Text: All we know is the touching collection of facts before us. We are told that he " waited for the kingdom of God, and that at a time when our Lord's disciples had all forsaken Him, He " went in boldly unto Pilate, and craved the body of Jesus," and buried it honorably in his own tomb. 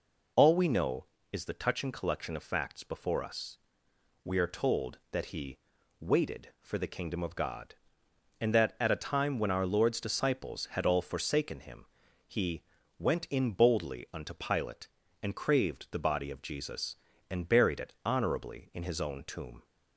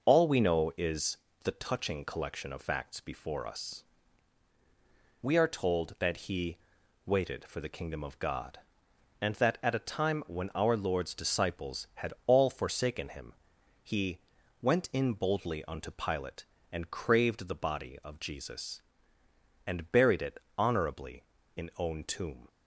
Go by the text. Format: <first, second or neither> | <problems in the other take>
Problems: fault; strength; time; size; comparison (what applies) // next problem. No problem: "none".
first | pauses between "is" and "the"; slight; at 1.1 s; 0.26 s long // pauses between "it" and "honorably"; slight; at 20.3 s; 0.18 s long // skips "his"; at 21.7 s